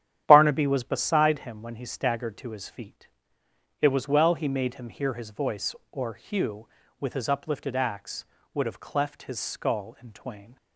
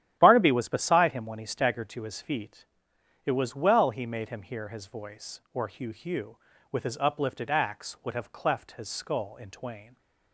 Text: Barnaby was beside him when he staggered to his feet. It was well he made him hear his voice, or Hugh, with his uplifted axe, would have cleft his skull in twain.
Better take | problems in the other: first | starts louder than the rest; strong; until 1.2 s; 11.5 dB; strong in the first // says "Hugh" twice; at 5.9 s

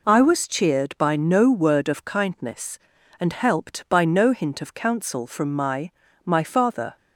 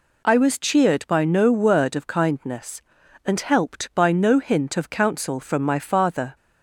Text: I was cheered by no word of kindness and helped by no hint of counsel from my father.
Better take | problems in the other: second | says "my" twice; at 6.2 s

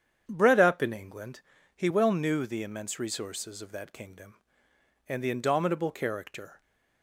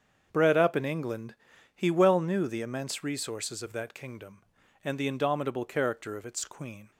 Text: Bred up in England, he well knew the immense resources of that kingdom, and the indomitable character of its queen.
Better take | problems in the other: second | starts louder than the rest; strong; until 1.2 s; 8.5 dB; also in the second // stops before "of its queen"; at 6.6 s

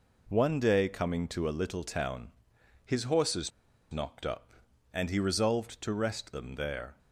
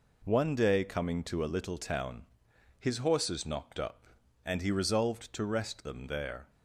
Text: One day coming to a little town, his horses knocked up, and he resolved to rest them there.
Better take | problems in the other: second | pauses between "horses" and "knocked"; at 3.4 s; 0.41 s long

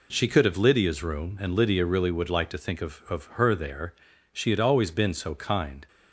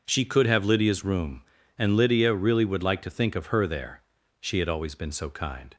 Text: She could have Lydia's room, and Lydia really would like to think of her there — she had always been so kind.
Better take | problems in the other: second | says "of" twice; at 3.0 s

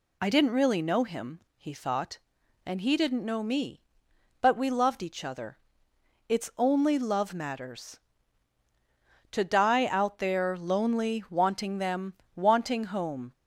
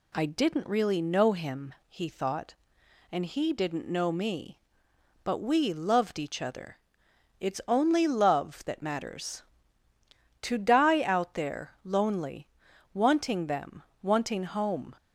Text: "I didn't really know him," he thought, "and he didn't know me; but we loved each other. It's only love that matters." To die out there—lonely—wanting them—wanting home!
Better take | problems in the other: second | skips "that"; at 7.3 s

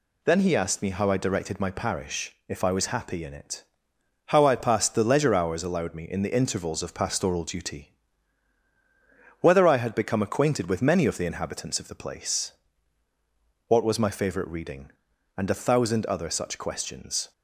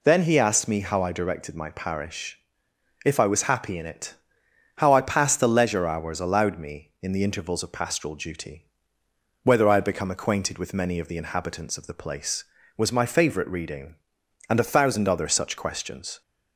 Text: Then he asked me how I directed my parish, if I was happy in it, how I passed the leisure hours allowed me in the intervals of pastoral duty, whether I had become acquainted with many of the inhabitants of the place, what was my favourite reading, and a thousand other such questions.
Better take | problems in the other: first | skips "what"; at 12.6 s

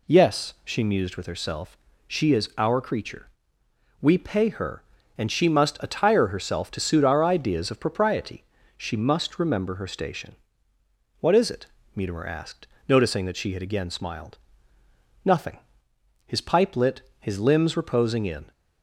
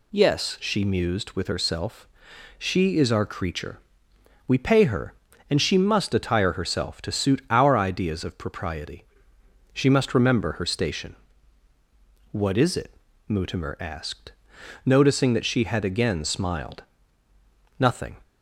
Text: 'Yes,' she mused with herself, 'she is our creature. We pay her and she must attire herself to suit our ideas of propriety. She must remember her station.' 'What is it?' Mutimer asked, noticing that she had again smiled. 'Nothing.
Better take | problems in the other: second | goes on to say "His pipe lit his limbs reposing in"; strong; from 16.2 s on; 2.2 s long

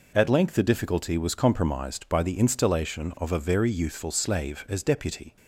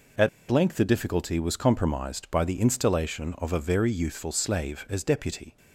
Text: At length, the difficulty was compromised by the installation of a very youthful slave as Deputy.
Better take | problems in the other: first | pauses between "At" and "length"; slight; at 0.2 s; 0.21 s long

